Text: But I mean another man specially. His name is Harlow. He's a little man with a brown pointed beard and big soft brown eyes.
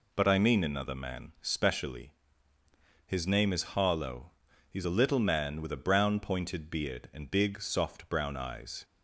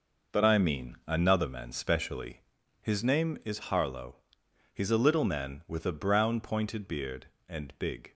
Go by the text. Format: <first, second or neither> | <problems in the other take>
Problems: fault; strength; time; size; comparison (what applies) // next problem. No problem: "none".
first | stops before "soft brown eyes"; at 8.0 s